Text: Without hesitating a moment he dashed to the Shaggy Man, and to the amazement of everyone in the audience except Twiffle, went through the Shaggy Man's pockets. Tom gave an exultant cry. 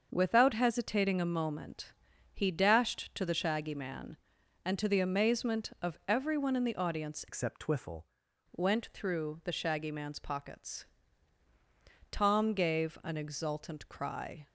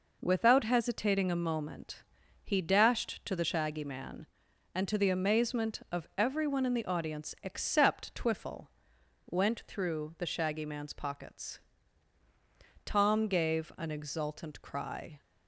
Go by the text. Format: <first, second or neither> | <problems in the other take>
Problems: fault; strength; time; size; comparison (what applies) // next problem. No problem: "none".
second | starts louder than the rest; until 1.1 s; 6.5 dB // pauses between "moment" and "he"; at 1.9 s; 0.42 s long; also in the second // changes voice from "except" to "Twiffle"; from 7.2 to 8.0 s; 0.8 s long